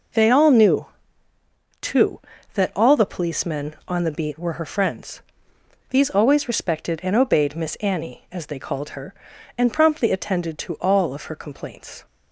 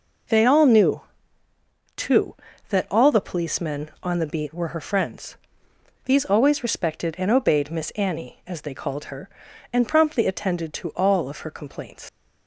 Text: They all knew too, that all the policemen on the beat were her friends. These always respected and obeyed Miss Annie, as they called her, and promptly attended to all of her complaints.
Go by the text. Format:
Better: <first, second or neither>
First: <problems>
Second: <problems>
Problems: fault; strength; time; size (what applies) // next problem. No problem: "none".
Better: first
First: pauses between "knew" and "too"; noticeable; at 0.8 s; 0.96 s long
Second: pauses between "knew" and "too"; noticeable; at 1.0 s; 0.96 s long // leaves "complaints" unfinished; at 12.0 s; 115 ms